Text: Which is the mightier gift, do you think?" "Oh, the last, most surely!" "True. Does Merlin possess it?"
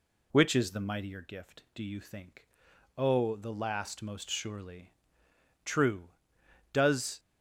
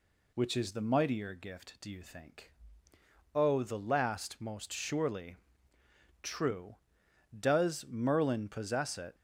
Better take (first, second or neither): second